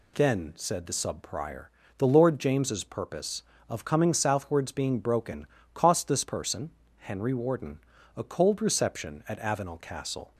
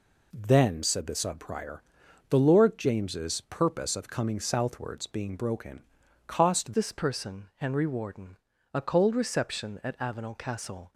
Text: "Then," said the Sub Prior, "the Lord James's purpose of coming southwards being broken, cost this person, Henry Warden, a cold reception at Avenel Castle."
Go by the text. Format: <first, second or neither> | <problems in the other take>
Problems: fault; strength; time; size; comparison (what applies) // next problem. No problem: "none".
first | changes voice at "this"; from 6.7 s on; 4.2 s long